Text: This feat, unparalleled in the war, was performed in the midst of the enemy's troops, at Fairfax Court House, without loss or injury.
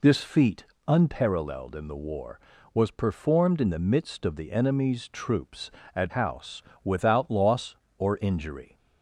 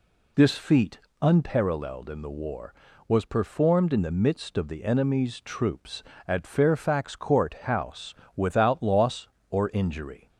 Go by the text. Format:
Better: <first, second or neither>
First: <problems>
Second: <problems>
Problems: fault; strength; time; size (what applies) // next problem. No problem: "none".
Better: second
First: skips "Fairfax Court"; at 6.1 s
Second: none